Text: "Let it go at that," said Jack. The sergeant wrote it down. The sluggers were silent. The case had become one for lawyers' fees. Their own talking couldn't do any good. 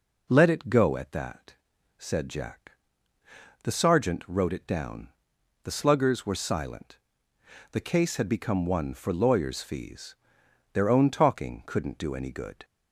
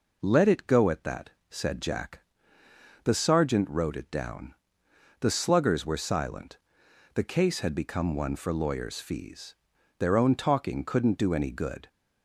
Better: neither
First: none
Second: none

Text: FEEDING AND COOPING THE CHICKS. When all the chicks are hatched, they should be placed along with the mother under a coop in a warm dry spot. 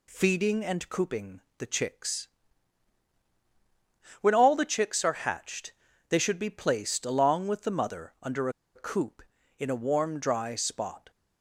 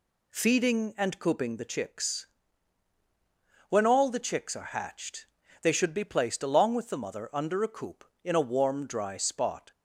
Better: second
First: pauses between "COOPING" and "THE"; slight; at 1.3 s; 0.20 s long // pauses between "under" and "a"; slight; at 8.4 s; 0.26 s long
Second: none

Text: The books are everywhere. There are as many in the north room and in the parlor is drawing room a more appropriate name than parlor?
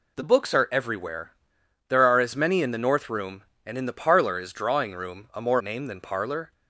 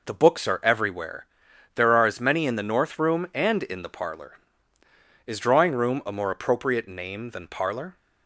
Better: second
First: skips "appropriate"; at 5.5 s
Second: none

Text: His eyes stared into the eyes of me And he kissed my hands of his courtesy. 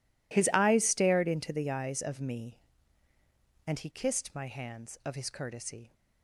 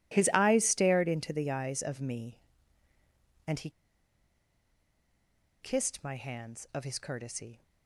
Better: first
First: none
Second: pauses between "he" and "kissed"; strong; at 3.7 s; 1.9 s long

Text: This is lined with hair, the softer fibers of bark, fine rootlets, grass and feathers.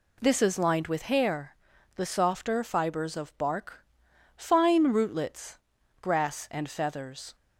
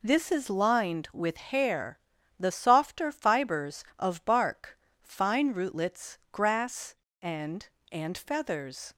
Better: first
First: none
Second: says "and" twice; at 7.9 s

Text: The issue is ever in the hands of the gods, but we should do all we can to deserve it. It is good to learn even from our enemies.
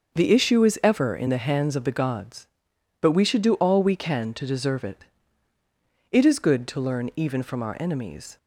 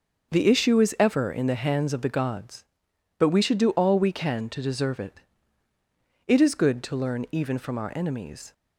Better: neither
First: starts louder than the rest; noticeable; until 1.1 s; 6 dB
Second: starts louder than the rest; noticeable; until 1.3 s; 6 dB

